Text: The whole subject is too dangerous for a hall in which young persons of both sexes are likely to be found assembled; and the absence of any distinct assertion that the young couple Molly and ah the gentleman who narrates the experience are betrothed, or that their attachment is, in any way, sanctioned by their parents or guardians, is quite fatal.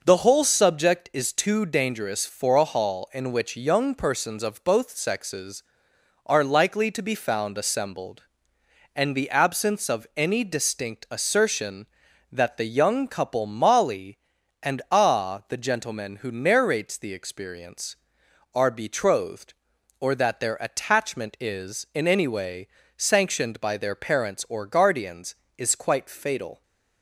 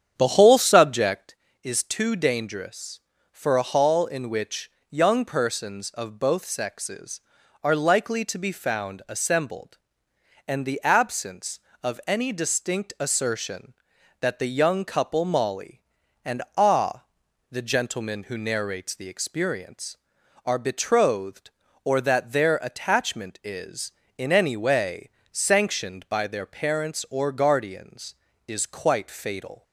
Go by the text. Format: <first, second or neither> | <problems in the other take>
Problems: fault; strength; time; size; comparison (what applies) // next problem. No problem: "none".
first | starts louder than the rest; strong; until 1.4 s; 8.5 dB // pauses between "which" and "young"; slight; at 4.7 s; 0.18 s long // pauses between "and" and "ah"; slight; at 16.4 s; 0.16 s long // pauses between "ah" and "the"; noticeable; at 17.0 s; 0.48 s long